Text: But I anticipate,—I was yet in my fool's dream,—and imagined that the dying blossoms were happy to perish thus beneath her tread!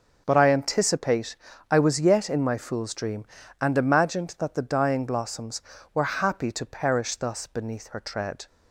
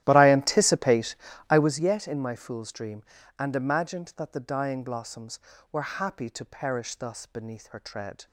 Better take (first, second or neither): first